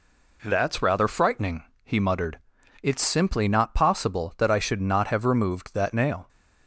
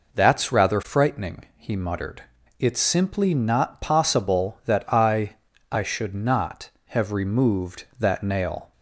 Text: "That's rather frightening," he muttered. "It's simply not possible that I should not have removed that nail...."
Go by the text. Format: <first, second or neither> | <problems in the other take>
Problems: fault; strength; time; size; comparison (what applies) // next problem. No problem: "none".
first | says "I" twice; at 5.7 s